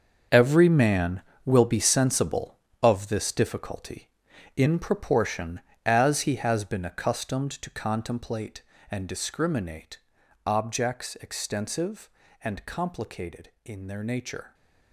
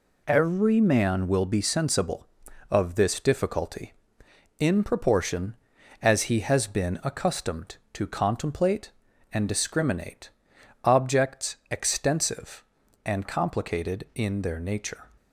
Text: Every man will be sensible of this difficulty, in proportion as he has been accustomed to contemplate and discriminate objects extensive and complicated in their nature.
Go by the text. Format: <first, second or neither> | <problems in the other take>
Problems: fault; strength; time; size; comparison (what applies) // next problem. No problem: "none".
second | gets quieter; strong; throughout; 12.5 dB // pauses between "discriminate" and "objects"; noticeable; at 9.9 s; 0.46 s long; noticeable in the second